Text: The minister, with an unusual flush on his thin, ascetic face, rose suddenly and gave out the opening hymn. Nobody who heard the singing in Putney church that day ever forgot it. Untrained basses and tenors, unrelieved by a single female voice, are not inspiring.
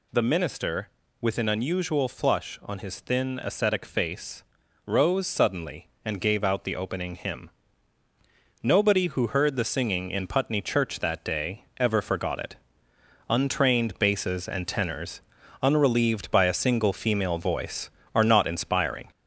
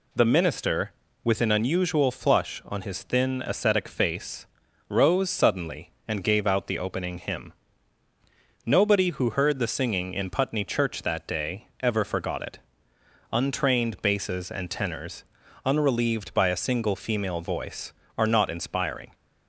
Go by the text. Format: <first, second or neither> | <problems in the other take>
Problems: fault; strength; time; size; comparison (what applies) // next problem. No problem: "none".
second | gets louder; throughout; 4 dB